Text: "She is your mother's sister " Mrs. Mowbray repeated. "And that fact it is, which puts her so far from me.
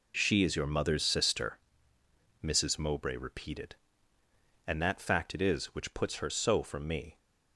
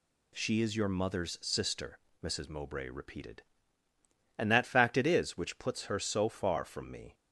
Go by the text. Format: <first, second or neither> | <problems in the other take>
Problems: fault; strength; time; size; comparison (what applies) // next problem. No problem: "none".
second | skips "far"; at 6.6 s